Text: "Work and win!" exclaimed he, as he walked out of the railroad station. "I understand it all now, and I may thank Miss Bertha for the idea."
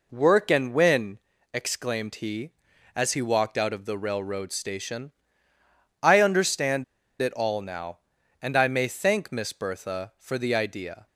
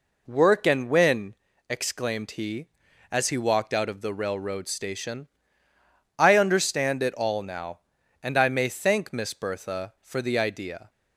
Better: second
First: pauses between "understand" and "it"; at 6.8 s; 0.37 s long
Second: none

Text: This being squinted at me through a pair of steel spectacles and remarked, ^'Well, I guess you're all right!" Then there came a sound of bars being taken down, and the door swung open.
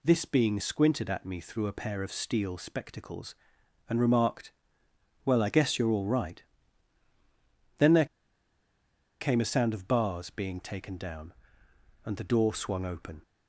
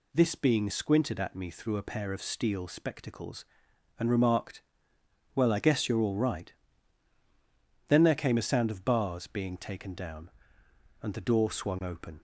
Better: second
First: pauses between "there" and "came"; at 8.0 s; 1.1 s long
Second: none

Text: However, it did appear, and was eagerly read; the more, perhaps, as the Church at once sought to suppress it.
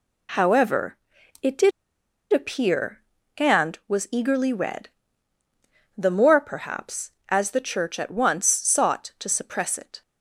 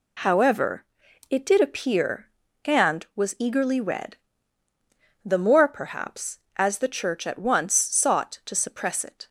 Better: second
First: pauses between "did" and "appear"; noticeable; at 1.7 s; 0.62 s long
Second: none

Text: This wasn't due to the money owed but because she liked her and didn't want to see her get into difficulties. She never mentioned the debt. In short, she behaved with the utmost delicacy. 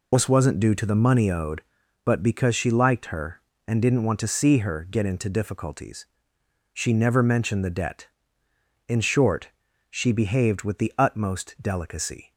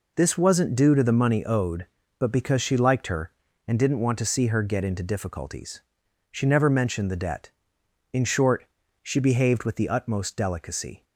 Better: second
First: loses the start of "This"; at 0.1 s; 45 ms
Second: none

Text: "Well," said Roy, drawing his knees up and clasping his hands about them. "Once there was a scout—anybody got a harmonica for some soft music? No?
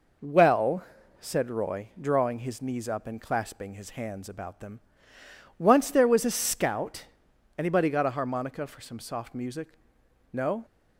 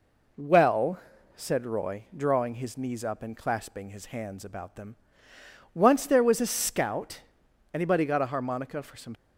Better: first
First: none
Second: stops before "soft music No"; at 9.1 s

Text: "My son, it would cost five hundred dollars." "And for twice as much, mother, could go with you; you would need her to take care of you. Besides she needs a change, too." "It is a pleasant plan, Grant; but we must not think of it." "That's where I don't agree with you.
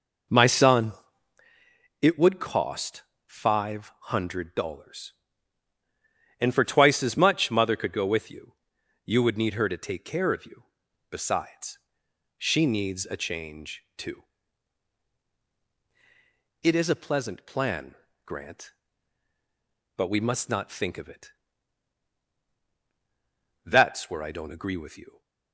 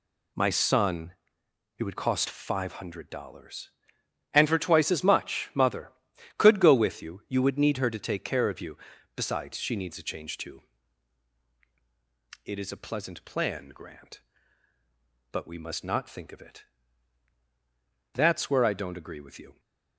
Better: second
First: starts louder than the rest; noticeable; until 1.5 s; 5 dB // pauses between "cost" and "five"; slight; at 3.0 s; 0.24 s long // pauses between "five" and "hundred"; slight; at 3.9 s; 0.22 s long // pauses between "Besides" and "she"; noticeable; at 11.7 s; 0.58 s long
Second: none

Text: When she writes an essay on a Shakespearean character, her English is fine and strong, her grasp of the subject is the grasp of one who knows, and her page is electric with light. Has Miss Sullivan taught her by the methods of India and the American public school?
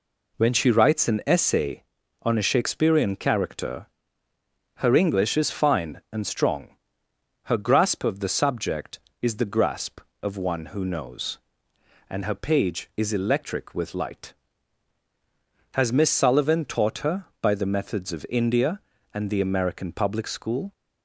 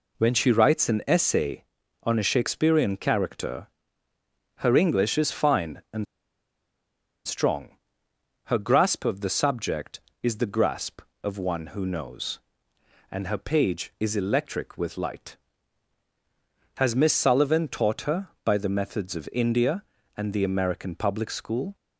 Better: first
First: none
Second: pauses between "and" and "strong"; at 6.0 s; 1.2 s long

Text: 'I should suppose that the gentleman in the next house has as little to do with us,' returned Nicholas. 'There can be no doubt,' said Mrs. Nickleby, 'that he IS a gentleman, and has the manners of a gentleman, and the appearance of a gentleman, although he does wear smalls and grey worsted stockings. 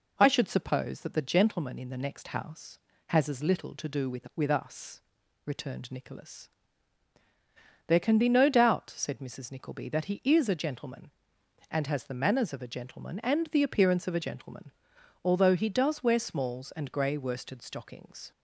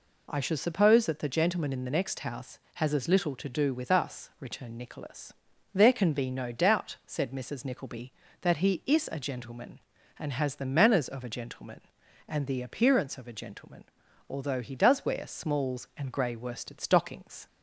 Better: second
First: says "with" twice; at 4.3 s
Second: none

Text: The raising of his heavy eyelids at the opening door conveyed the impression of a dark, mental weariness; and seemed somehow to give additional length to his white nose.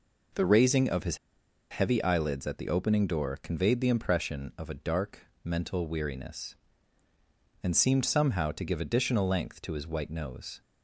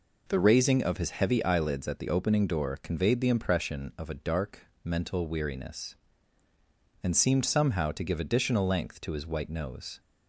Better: second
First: pauses between "his" and "heavy"; noticeable; at 1.1 s; 0.53 s long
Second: none

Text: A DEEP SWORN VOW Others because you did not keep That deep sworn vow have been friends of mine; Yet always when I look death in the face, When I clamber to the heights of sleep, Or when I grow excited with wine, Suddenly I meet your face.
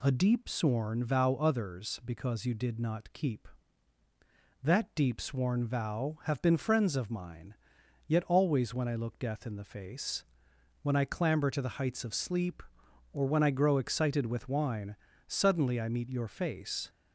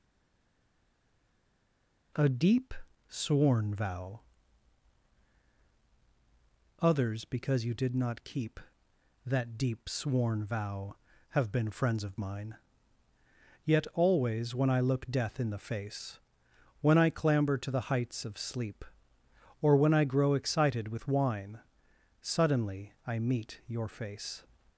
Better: first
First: none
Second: stays silent before the first word; until 2.1 s; 2.1 s long // pauses between "DEEP" and "SWORN"; slight; at 2.7 s; 0.34 s long // pauses between "VOW" and "Others"; strong; at 4.1 s; 2.6 s long // pauses between "Suddenly" and "I"; slight; at 22.9 s; 0.16 s long

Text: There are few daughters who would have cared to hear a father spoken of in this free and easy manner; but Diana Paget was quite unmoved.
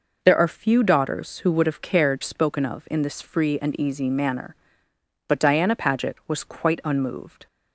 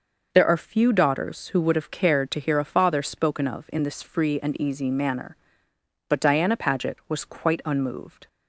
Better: second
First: skips "to hear a father"; at 2.2 s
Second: none

